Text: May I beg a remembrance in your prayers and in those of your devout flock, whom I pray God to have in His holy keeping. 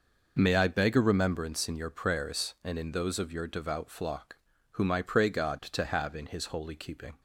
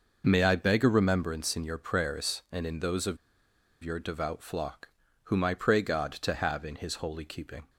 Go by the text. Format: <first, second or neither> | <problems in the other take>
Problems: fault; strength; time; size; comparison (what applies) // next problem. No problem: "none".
first | pauses between "of" and "your"; noticeable; at 3.1 s; 0.66 s long